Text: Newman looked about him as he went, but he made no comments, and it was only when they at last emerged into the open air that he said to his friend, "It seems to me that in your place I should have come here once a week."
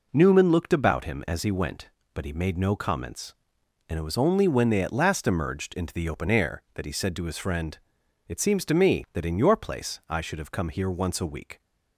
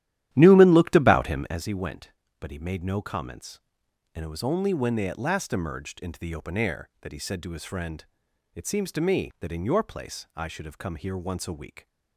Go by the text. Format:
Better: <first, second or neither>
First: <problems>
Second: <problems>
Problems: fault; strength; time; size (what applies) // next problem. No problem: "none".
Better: first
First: none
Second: starts louder than the rest; strong; until 1.6 s; 12 dB